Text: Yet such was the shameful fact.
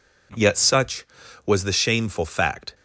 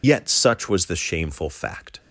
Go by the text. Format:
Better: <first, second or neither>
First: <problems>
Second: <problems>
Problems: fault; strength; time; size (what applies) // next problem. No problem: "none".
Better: first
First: none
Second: loses the start of "Yet"; at 0.0 s; 45 ms